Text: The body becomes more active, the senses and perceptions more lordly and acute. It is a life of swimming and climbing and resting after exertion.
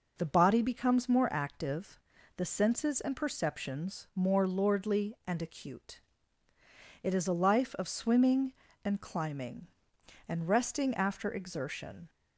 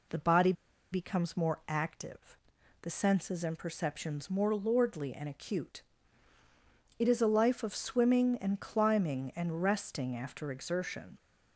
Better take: first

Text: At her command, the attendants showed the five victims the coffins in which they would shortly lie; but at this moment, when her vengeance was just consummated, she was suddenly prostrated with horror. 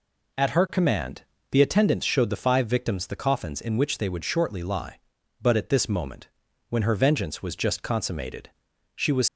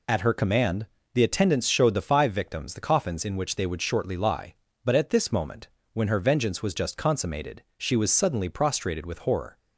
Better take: second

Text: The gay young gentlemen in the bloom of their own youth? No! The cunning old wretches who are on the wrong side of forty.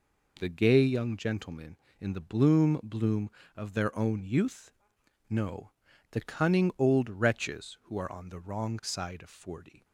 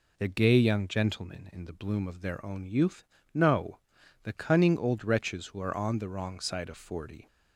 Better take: second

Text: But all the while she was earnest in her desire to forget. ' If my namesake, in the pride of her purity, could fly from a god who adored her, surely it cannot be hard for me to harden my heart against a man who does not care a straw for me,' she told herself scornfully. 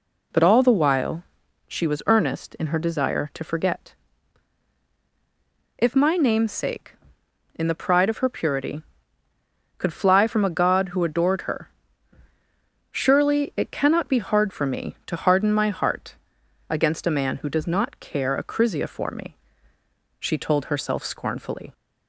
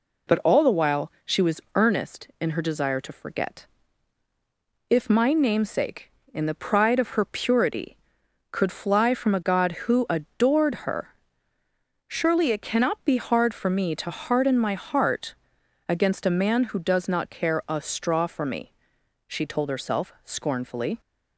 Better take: second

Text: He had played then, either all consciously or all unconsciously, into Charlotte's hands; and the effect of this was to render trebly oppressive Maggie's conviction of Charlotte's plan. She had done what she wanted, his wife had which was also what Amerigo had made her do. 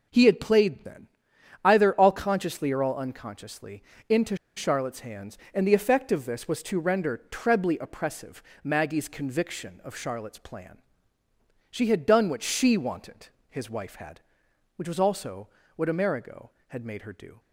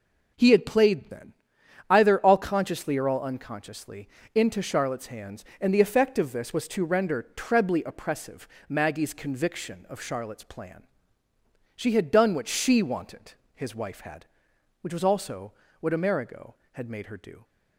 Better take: second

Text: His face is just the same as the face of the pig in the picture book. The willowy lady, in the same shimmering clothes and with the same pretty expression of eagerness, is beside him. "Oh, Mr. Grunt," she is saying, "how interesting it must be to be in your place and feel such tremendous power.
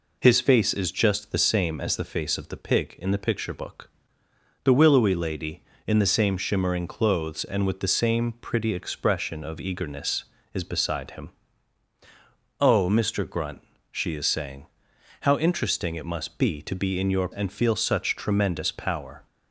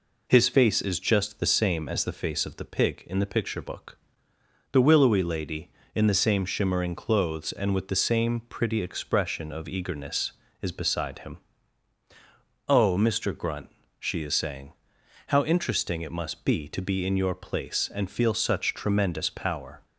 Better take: second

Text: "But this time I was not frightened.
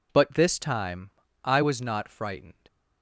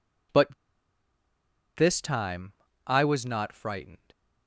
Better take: first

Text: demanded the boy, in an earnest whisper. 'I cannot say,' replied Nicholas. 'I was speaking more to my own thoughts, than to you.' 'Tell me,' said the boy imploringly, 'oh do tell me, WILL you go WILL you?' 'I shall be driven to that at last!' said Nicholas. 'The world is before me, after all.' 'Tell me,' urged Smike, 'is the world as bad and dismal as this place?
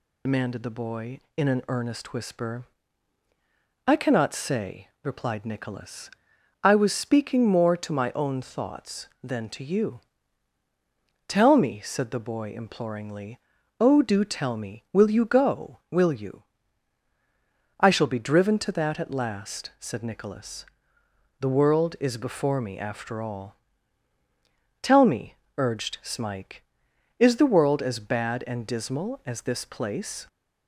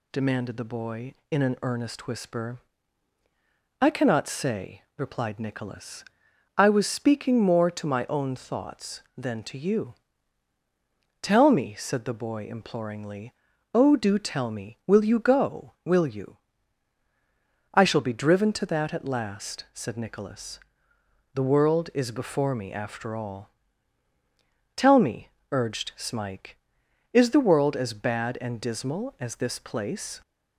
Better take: second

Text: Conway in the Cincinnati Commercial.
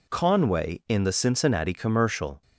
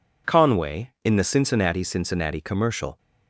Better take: first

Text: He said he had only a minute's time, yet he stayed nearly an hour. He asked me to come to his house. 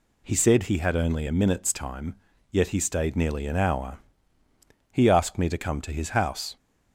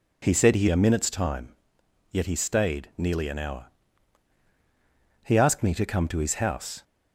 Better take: first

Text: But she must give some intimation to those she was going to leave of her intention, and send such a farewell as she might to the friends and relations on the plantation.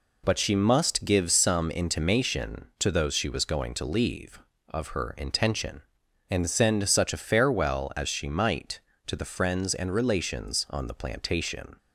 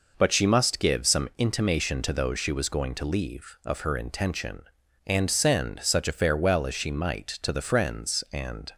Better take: first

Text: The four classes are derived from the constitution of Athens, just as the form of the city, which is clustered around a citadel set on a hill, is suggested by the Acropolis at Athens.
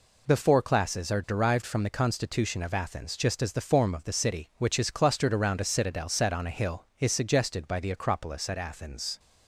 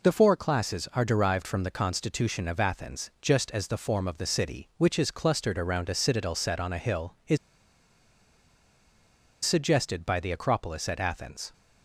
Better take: first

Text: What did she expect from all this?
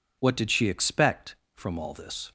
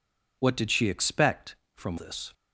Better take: first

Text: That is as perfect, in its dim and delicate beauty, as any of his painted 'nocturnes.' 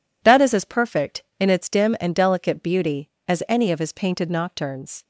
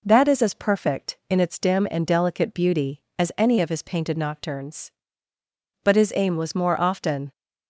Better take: first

